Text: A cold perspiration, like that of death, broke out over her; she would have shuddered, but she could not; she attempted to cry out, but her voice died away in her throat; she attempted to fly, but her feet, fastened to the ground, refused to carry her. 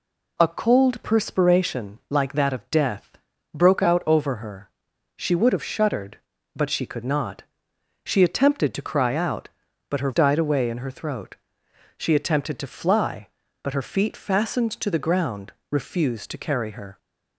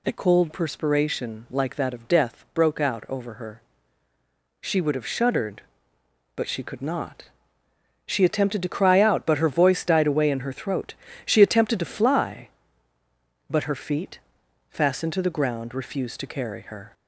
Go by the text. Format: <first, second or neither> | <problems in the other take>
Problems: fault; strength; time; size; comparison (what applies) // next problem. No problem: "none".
second | skips "voice"; at 10.1 s